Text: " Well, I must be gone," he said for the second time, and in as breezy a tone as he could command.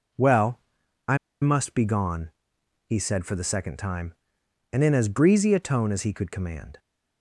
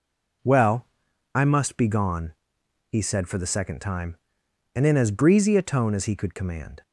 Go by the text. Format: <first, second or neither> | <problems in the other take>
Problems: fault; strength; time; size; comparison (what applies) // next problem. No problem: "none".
second | pauses between "I" and "must"; slight; at 1.1 s; 0.25 s long